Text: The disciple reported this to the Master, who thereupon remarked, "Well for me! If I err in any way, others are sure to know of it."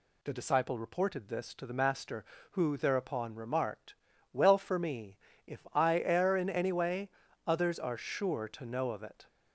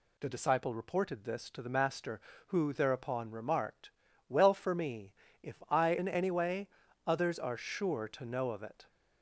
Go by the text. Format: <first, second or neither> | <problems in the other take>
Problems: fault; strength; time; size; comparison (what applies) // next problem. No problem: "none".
first | skips "err"; at 5.9 s